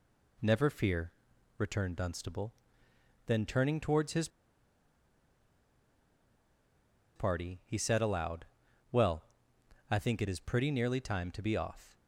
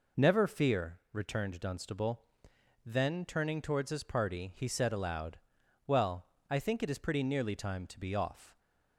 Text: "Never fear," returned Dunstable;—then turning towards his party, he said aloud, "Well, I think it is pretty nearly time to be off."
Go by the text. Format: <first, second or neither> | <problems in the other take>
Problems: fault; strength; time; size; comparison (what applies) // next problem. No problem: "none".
second | pauses between "his" and "party"; strong; at 4.2 s; 2.8 s long